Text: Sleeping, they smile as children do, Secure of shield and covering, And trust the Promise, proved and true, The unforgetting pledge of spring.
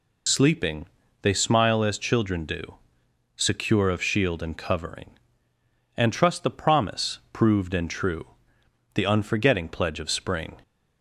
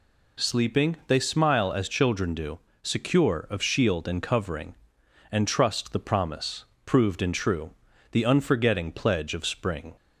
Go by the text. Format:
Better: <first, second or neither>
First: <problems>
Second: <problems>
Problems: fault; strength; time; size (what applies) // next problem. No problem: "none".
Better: second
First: loses the start of "Sleeping"; at 0.2 s; 55 ms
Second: none